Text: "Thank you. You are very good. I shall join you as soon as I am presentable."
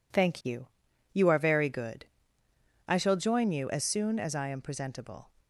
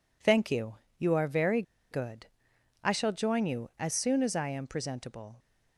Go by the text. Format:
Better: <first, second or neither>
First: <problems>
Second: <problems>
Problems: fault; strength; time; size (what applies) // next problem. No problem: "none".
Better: first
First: none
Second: pauses between "very" and "good"; slight; at 1.6 s; 0.28 s long